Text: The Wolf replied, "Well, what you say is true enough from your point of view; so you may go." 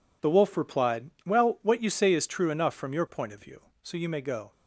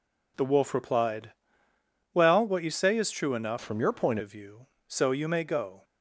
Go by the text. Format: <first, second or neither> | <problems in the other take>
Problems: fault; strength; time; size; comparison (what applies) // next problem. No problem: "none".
first | changes voice from "from" to "point"; from 3.6 to 4.1 s; 0.5 s long